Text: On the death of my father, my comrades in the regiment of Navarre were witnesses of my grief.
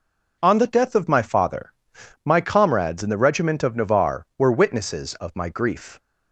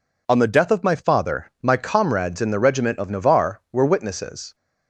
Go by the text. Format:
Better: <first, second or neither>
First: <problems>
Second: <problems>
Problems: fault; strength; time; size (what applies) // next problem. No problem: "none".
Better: first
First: none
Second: stops before "of my grief"; at 4.5 s